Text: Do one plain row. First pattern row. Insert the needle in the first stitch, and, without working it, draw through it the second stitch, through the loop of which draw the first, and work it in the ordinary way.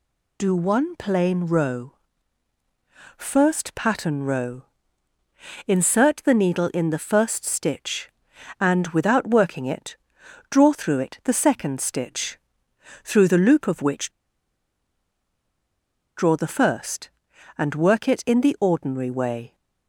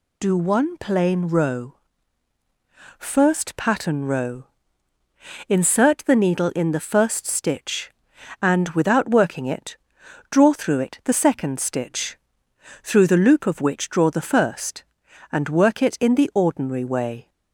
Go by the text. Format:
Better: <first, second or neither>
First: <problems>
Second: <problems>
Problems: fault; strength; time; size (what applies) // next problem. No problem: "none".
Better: second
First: pauses between "which" and "draw"; strong; at 14.0 s; 2.0 s long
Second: none